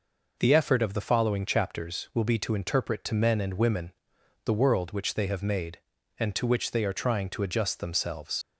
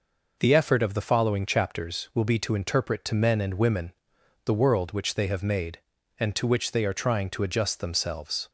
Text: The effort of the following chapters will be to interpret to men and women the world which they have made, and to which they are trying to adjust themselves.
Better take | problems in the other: second | pauses between "women" and "the"; noticeable; at 3.9 s; 0.50 s long; noticeable in the second // leaves "themselves" unfinished; at 8.4 s; 80 ms

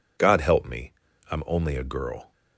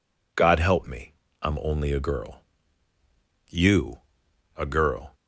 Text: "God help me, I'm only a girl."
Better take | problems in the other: first | goes on to say "You a girl"; from 3.5 s on; 1.6 s long

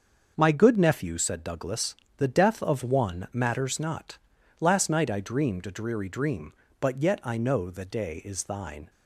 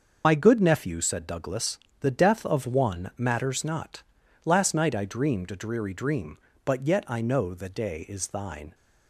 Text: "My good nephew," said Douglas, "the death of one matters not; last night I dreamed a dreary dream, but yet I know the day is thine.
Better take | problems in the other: first | loses the start of "My"; at 0.2 s; 55 ms // starts louder than the rest; until 1.2 s; 6 dB; also in the first

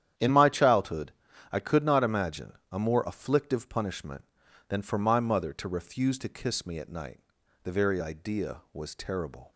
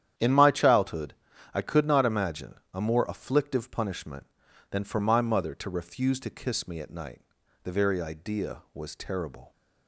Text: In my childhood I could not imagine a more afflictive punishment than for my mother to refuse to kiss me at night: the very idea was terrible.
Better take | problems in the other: neither | starts louder than the rest; strong; the same in both // pauses between "childhood" and "I"; the same in both // pauses between "imagine" and "a"; slight; the same in both

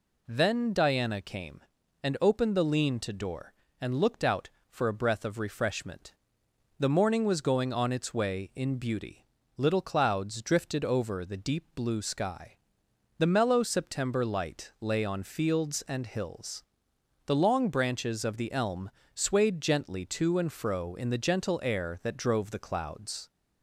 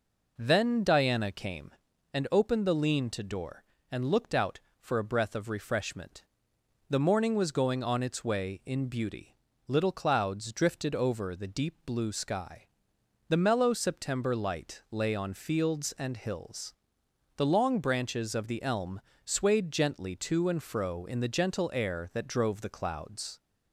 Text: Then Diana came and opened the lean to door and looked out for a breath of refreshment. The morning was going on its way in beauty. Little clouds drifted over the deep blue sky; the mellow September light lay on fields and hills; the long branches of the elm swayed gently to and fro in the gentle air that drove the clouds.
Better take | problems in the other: first | starts louder than the rest; noticeable; until 2.0 s; 4.5 dB // pauses between "elm" and "swayed"; slight; at 19.0 s; 0.24 s long; slight in the first

